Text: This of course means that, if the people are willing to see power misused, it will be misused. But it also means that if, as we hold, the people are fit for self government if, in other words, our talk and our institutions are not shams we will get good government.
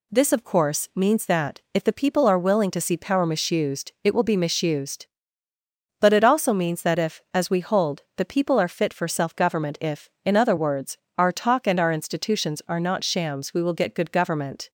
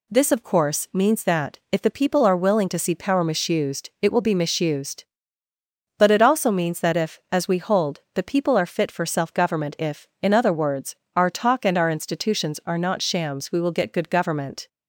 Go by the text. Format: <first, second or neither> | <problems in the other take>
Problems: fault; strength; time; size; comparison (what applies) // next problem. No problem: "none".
neither | none